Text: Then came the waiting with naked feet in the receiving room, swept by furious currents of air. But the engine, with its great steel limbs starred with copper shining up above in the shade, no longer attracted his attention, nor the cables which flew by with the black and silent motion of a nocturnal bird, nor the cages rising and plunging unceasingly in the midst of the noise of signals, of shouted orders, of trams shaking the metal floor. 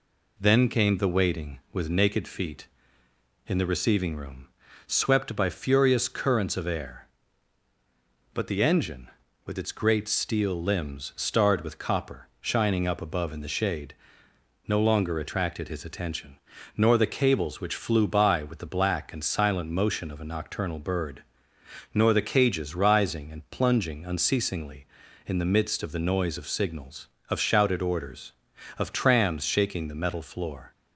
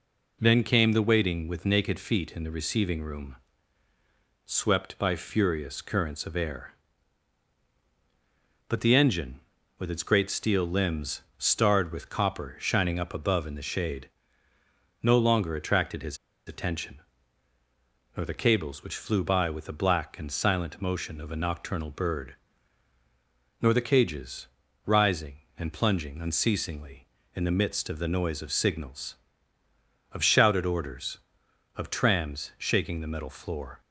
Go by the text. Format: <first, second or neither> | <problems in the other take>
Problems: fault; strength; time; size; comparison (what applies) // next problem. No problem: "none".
first | pauses between "his" and "attention"; slight; at 16.1 s; 0.31 s long // pauses between "cages" and "rising"; at 24.4 s; 0.40 s long